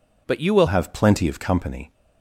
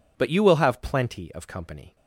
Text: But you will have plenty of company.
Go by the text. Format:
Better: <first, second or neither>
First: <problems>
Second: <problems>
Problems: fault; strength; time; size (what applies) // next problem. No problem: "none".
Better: second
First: changes voice at "have"; from 0.6 s on; 1.3 s long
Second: none